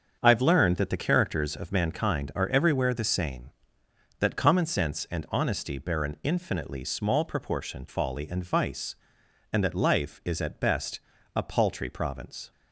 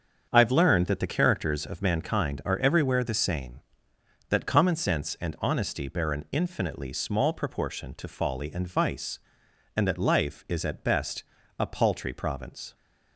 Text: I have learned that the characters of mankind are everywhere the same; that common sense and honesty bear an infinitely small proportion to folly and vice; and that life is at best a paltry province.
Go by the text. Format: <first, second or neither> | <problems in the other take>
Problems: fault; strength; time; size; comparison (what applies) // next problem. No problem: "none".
second | starts louder than the rest; until 1.2 s; 7 dB; strong in the second // skips "to"; at 7.8 s // pauses between "best" and "a"; at 10.9 s; 0.38 s long; also in the second